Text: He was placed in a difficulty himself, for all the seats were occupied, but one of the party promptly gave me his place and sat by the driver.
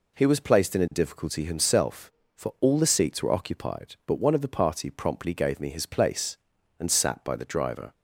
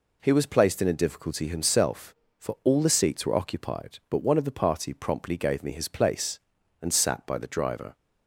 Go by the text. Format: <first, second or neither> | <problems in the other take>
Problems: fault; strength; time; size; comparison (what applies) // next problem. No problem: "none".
neither | none